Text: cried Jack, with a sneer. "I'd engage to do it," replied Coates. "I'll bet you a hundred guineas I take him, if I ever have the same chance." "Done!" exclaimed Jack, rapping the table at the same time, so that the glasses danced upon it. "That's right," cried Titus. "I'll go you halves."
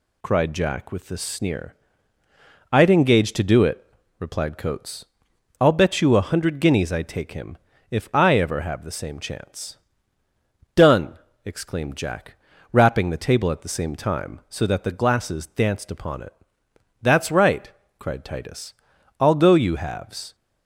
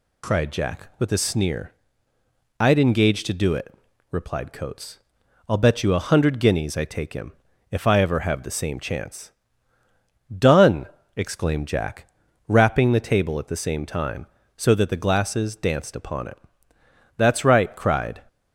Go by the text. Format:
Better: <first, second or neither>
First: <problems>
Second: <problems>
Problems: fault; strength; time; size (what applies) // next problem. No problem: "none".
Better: first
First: none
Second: stops before "Titus I'll go you halves"; at 18.2 s